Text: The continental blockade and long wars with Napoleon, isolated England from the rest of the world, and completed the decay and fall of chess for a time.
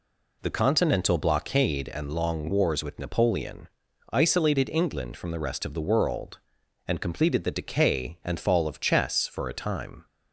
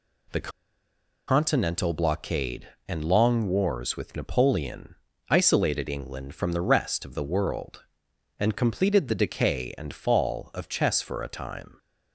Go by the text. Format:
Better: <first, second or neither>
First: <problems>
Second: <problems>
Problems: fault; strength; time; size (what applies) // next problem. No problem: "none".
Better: first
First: none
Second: pauses between "The" and "continental"; noticeable; at 0.5 s; 0.76 s long